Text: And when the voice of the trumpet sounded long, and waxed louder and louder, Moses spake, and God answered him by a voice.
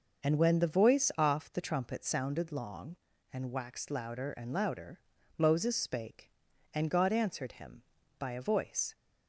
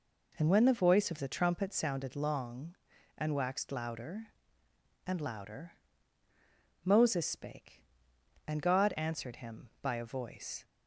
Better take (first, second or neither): second